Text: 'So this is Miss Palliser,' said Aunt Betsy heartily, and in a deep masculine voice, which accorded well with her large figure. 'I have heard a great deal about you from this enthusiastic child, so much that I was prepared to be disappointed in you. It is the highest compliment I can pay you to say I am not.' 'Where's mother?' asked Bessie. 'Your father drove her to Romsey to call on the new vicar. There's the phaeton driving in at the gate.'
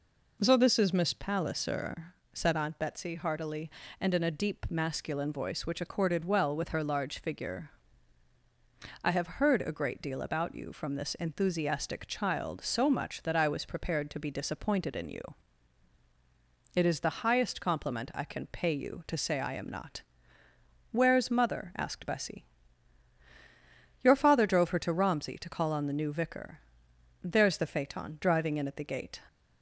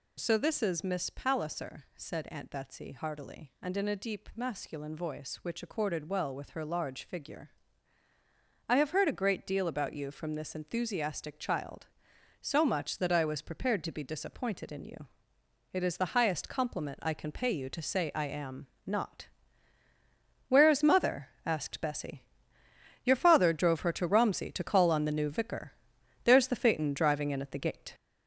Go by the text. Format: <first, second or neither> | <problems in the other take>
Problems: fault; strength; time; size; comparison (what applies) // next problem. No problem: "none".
first | gets louder; noticeable; throughout; 5.5 dB // pauses between "am" and "not"; slight; at 18.6 s; 0.18 s long